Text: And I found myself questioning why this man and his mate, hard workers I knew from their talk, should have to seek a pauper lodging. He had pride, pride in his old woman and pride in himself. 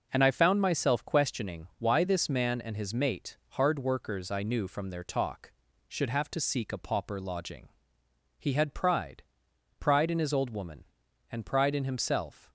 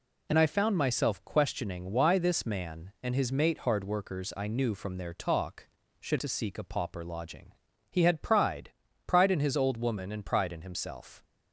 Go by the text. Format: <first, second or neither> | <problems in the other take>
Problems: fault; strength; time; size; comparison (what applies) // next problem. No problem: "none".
first | skips "have"; at 6.1 s